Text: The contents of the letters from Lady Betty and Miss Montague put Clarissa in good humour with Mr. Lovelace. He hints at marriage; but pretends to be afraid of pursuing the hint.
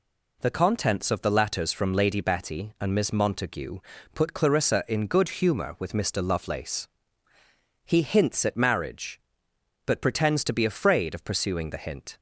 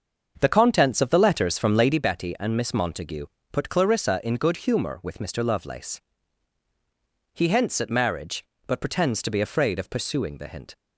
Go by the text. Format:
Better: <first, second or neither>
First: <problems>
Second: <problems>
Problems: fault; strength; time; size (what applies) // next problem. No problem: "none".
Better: first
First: pauses between "Montague" and "put"; slight; at 3.7 s; 0.34 s long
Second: starts louder than the rest; until 2.0 s; 6.5 dB // pauses between "Montague" and "put"; slight; at 3.2 s; 0.28 s long